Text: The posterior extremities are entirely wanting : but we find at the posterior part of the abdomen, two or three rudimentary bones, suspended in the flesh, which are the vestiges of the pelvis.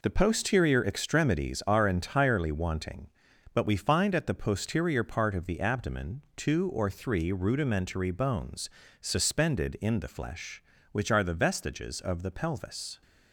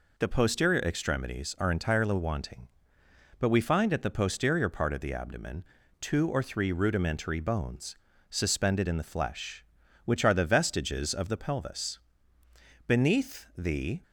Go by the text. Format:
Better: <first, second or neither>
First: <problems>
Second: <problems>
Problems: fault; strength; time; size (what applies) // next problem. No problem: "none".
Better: first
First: none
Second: goes on to say "Beneath the"; noticeable; from 12.8 s on; 1.1 s long